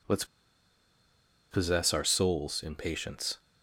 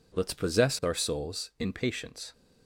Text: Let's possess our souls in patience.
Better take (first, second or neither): second